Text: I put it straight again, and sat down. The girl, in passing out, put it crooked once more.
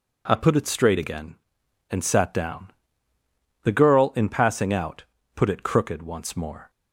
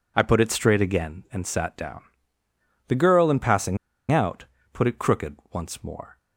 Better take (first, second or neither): first